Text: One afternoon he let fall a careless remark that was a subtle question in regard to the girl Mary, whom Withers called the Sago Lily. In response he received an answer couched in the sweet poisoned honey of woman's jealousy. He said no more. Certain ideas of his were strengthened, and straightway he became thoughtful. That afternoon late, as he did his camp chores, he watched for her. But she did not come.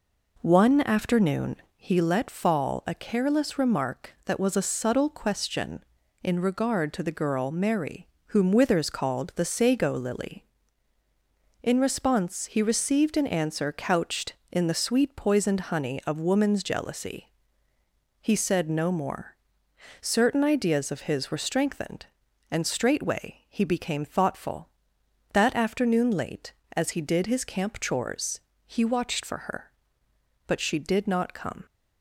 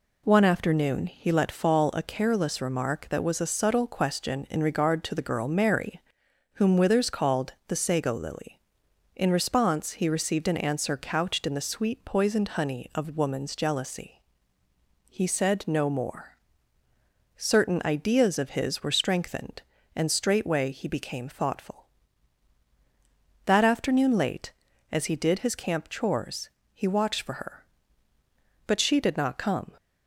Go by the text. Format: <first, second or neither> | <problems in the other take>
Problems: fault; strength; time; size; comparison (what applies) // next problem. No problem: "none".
second | starts louder than the rest; noticeable; until 2.2 s; 4.5 dB // pauses between "afternoon" and "he"; slight; at 1.5 s; 0.20 s long